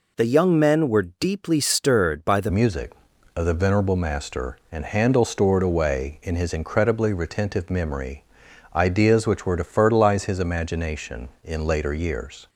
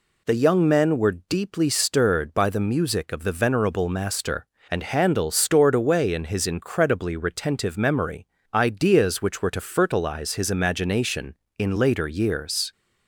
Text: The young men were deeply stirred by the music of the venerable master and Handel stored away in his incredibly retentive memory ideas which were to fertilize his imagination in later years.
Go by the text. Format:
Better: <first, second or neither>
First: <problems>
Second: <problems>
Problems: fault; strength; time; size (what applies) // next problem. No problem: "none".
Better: second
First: changes voice at "music"; from 2.4 s on; 10.0 s long // pauses between "memory" and "ideas"; noticeable; at 8.2 s; 0.52 s long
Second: pauses between "memory" and "ideas"; slight; at 8.2 s; 0.28 s long